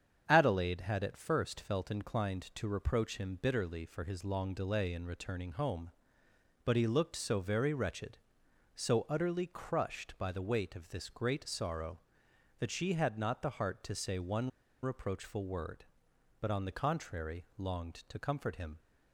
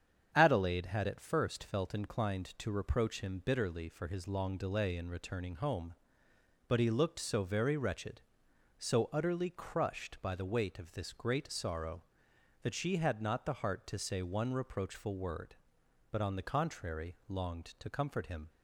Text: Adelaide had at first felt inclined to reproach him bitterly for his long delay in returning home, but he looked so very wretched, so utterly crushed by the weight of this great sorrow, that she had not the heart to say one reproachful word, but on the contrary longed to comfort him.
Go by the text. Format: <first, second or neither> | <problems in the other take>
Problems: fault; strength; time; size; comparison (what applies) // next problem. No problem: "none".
second | starts louder than the rest; strong; until 1.2 s; 8 dB; strong in the second // pauses between "one" and "reproachful"; slight; at 14.4 s; 0.33 s long